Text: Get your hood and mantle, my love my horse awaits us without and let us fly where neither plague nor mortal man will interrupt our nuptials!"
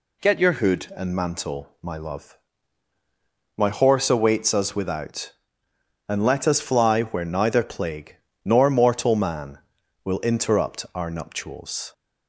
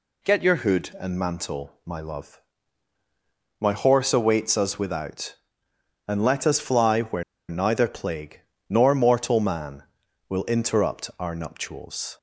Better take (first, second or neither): first